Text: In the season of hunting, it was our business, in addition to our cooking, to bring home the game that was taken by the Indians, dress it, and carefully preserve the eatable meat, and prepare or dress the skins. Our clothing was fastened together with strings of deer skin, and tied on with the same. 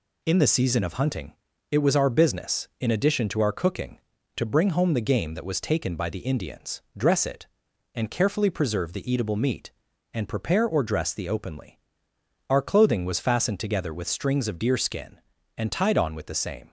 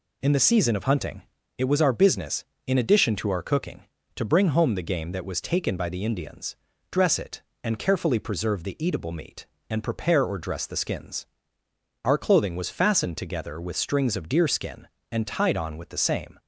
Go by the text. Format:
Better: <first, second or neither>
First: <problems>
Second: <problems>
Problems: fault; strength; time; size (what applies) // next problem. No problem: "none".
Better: second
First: says "openly" for "skins"; at 11.2 s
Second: none